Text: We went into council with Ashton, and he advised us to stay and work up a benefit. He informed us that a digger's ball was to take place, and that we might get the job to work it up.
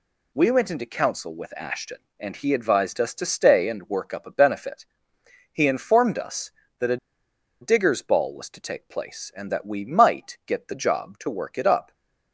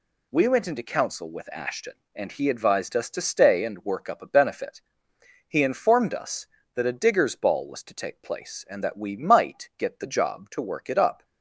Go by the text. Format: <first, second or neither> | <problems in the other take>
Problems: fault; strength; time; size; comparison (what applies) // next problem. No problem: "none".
second | pauses between "a" and "digger's"; noticeable; at 6.9 s; 0.64 s long // stays silent after the last word; slight; from 11.8 s on; 0.5 s long